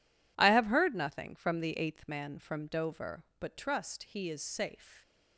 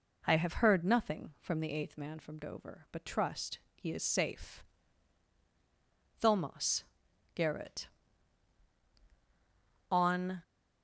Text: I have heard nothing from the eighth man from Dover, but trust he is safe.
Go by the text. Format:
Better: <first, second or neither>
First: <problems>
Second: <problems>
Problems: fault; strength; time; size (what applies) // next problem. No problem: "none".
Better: first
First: none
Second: pauses between "trust" and "he"; slight; at 3.5 s; 0.16 s long // goes on to say "THOMAS GARRETT On"; strong; from 6.2 s on; 4.2 s long